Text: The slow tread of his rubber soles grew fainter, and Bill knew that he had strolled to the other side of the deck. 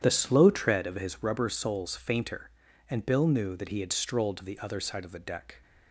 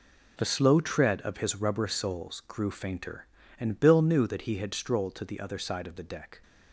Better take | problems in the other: second | starts louder than the rest; strong; until 1.0 s; 9.5 dB // skips "grew"; at 1.9 s

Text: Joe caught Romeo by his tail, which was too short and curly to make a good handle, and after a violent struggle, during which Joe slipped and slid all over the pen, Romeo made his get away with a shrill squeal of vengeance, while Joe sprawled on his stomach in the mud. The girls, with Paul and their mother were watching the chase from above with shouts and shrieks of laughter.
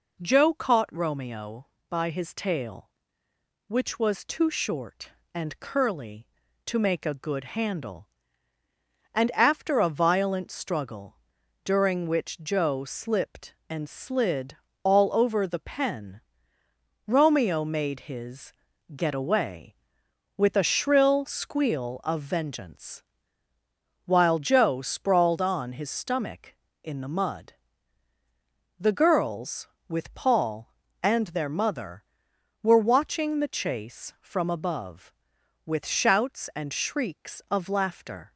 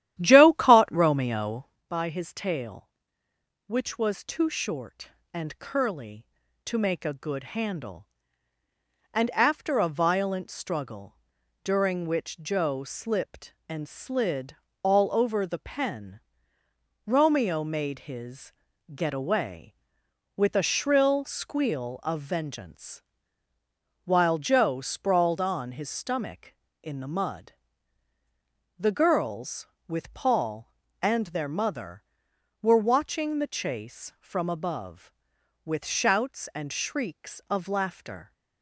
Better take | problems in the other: first | starts louder than the rest; strong; until 1.8 s; 12 dB // pauses between "slid" and "all"; slight; at 14.5 s; 0.26 s long; slight in the first // pauses between "his" and "get"; at 18.5 s; 0.44 s long; also in the first

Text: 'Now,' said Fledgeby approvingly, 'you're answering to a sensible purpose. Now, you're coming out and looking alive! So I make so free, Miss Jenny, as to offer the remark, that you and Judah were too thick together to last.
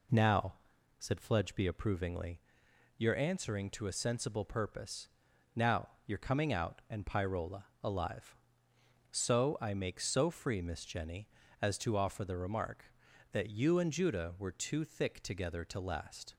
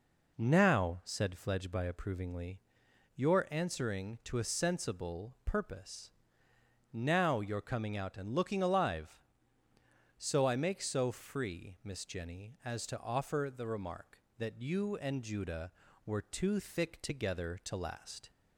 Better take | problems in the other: second | says "pyrola" for "looking"; at 7.0 s

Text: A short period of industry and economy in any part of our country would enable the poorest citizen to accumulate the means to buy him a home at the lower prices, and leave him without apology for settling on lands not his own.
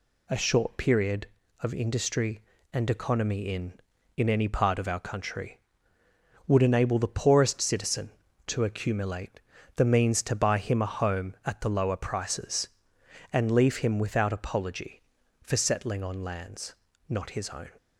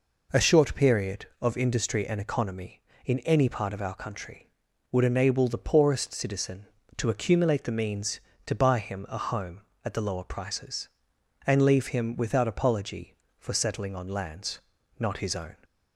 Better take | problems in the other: second | says "in" twice; at 4.1 s // pauses between "accumulate" and "the"; slight; at 9.4 s; 0.36 s long // pauses between "lands" and "not"; slight; at 16.7 s; 0.34 s long; also in the second

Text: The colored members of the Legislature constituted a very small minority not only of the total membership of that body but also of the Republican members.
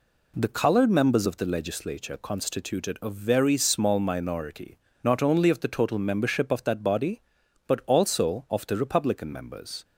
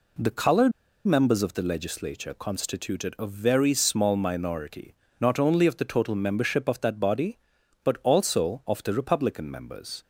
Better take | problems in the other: first | pauses between "colored" and "members"; slight; at 0.7 s; 0.35 s long // pauses between "minority" and "not"; slight; at 4.9 s; 0.26 s long; slight in the first

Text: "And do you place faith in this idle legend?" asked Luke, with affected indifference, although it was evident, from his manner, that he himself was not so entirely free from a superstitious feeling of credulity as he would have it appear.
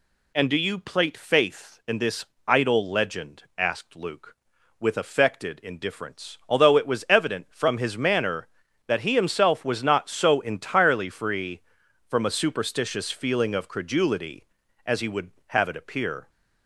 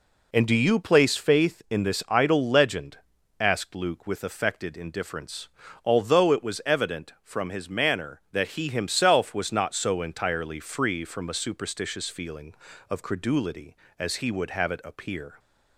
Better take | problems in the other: second | says "plate" for "place"; at 0.7 s // pauses between "this" and "idle"; slight; at 2.2 s; 0.20 s long

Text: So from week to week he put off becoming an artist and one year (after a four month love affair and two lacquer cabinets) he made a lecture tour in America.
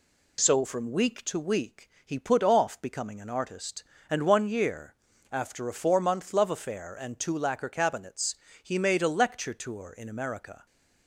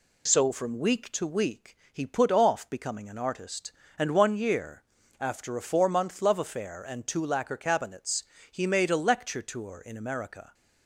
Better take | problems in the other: neither | pauses between "week" and "he"; slight; the same in both

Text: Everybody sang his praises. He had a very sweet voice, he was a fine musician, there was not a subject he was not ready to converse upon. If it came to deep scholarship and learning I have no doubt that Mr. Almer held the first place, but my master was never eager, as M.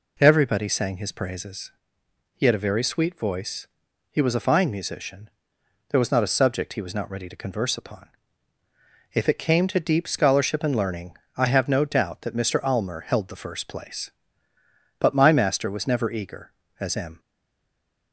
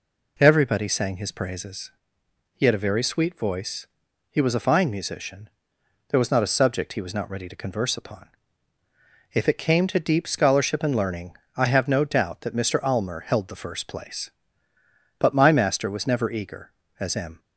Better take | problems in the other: second | pauses between "learning" and "I"; slight; at 11.1 s; 0.20 s long; slight in the second // stays silent after the last word; slight; from 17.1 s on; 1.0 s long

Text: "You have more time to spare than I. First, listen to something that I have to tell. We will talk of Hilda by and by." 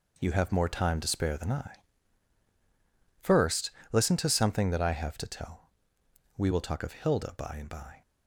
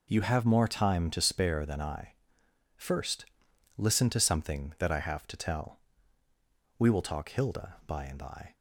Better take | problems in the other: first | skips "of"; at 7.2 s

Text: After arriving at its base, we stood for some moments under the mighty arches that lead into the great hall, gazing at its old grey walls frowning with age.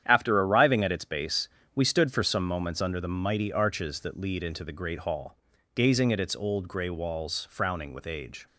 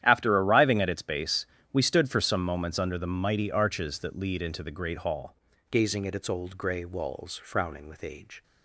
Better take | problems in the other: first | starts louder than the rest; strong; until 1.0 s; 11 dB; strong in the first // changes voice at "gazing"; from 5.6 s on; 2.8 s long

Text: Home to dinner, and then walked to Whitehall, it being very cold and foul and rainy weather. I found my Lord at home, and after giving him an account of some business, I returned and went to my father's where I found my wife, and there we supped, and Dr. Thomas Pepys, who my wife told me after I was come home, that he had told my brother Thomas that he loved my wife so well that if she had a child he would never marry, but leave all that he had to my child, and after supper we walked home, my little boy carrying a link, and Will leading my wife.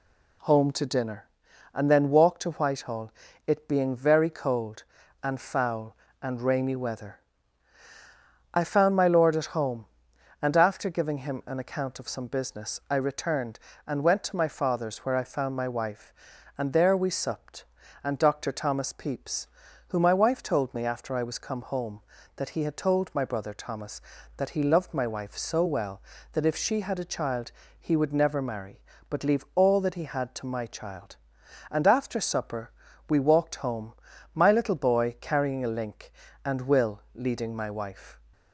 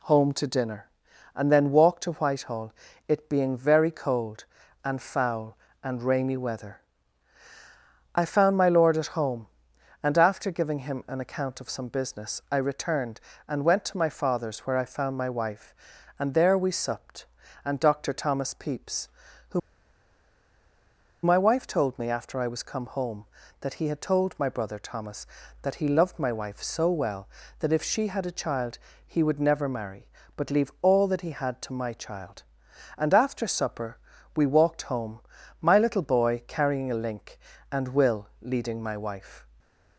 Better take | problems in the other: first | pauses between "who" and "my"; strong; at 19.5 s; 1.6 s long // pauses between "child" and "he"; slight; at 28.7 s; 0.28 s long; slight in the first // pauses between "supper" and "we"; at 33.9 s; 0.38 s long; also in the first // stays silent after the last word; slight; from 39.4 s on; 0.5 s long

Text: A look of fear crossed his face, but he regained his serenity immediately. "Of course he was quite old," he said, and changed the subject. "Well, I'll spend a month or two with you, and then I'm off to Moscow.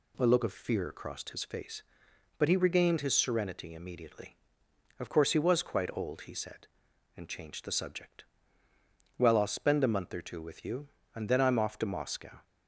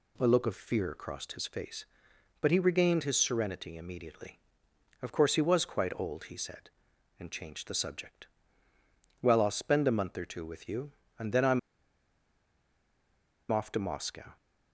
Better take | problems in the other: first | pauses between "I'm" and "off"; strong; at 11.5 s; 1.9 s long

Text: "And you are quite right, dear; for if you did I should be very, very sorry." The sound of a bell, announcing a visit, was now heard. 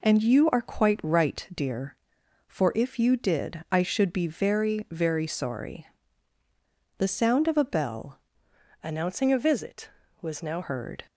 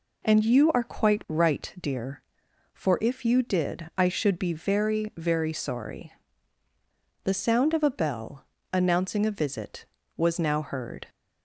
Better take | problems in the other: second | changes voice from "announcing" to "now"; from 8.8 to 10.6 s; 1.8 s long

